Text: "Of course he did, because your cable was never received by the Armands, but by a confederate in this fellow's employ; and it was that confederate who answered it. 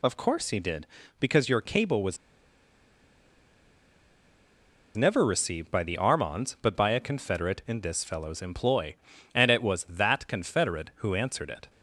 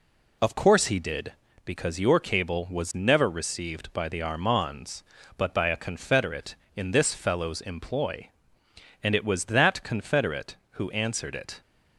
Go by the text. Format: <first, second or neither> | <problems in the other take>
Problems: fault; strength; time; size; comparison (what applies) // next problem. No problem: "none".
second | pauses between "was" and "never"; strong; at 2.1 s; 2.8 s long